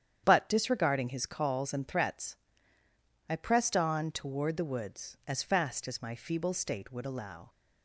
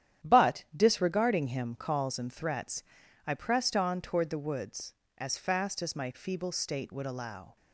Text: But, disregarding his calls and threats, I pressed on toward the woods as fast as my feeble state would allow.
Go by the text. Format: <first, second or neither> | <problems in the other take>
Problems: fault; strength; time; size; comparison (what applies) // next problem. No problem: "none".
first | starts louder than the rest; strong; until 1.3 s; 10.5 dB; strong in the first // says "him" for "his"; at 1.4 s